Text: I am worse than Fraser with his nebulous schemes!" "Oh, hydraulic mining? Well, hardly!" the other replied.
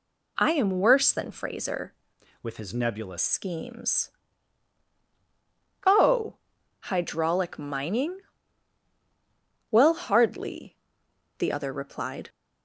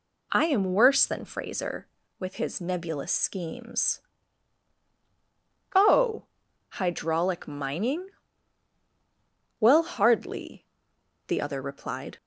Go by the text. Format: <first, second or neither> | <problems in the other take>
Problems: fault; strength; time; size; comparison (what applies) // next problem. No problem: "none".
second | changes voice from "with" to "nebulous"; from 2.4 to 3.1 s; 0.7 s long